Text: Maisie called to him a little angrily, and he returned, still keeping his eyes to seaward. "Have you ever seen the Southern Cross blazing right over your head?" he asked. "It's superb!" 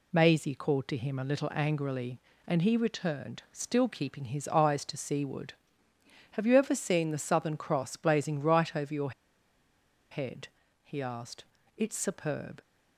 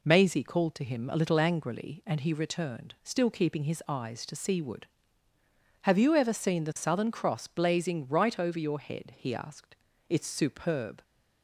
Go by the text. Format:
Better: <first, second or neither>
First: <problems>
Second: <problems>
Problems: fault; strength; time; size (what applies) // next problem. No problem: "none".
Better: second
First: pauses between "your" and "head"; at 9.1 s; 1.0 s long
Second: none